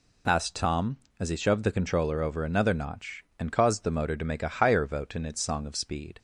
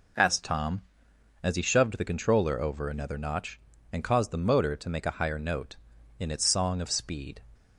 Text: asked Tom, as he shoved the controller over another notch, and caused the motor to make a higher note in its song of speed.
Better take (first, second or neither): second